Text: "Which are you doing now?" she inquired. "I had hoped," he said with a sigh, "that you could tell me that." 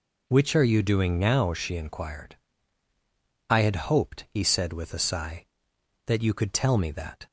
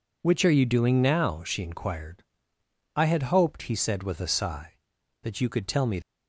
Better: first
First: none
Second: stops before "that"; at 6.0 s

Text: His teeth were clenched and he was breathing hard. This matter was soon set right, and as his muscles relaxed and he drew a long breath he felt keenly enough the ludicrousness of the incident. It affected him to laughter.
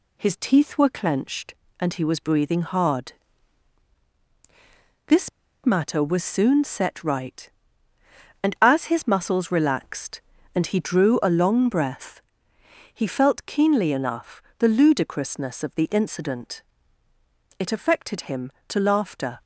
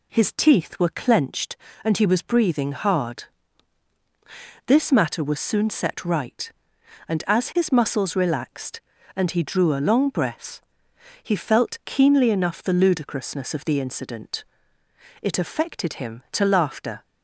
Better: second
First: pauses between "This" and "matter"; slight; at 5.2 s; 0.35 s long // pauses between "breath" and "he"; noticeable; at 12.1 s; 0.74 s long // pauses between "enough" and "the"; slight; at 14.4 s; 0.16 s long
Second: pauses between "breath" and "he"; noticeable; at 10.6 s; 0.60 s long

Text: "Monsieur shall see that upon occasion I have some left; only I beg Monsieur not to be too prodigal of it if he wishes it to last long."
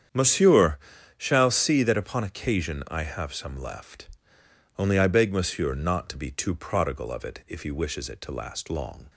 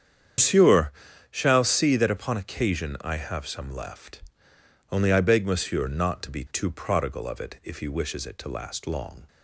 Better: first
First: starts louder than the rest; strong; until 1.5 s; 8.5 dB // pauses between "Monsieur" and "shall"; at 0.7 s; 0.40 s long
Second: loses the start of "Monsieur"; at 0.3 s; 135 ms // starts louder than the rest; strong; until 1.7 s; 8.5 dB // pauses between "Monsieur" and "shall"; at 0.9 s; 0.40 s long

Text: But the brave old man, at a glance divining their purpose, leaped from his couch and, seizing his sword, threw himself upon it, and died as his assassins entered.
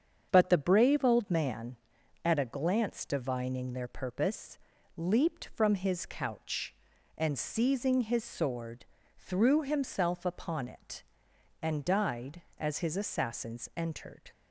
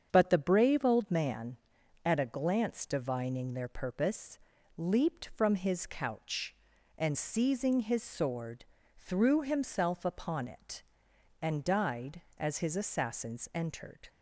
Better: neither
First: starts louder than the rest; strong; until 1.3 s; 7.5 dB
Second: starts louder than the rest; strong; until 1.1 s; 7.5 dB

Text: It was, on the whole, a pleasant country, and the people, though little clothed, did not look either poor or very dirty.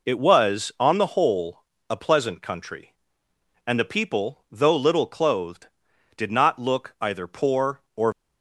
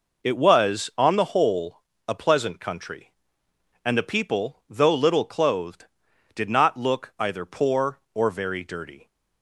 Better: second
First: stops before "very dirty"; at 8.1 s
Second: none

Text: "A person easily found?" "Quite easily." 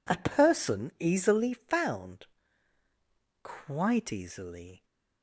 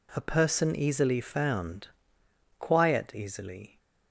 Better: first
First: none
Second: says "Quiet" for "Quite"; at 2.5 s

